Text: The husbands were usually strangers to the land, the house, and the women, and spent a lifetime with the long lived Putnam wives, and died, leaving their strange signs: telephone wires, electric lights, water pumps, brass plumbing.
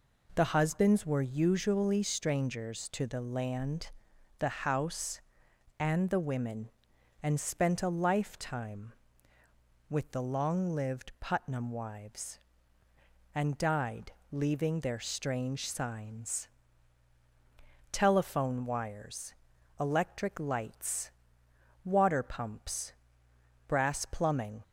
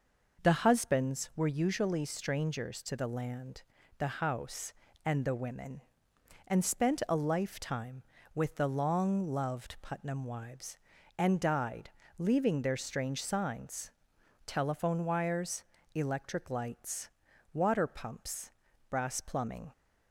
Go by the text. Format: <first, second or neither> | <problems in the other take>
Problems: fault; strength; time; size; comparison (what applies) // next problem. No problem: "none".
first | says "loved" for "lived"; at 9.2 s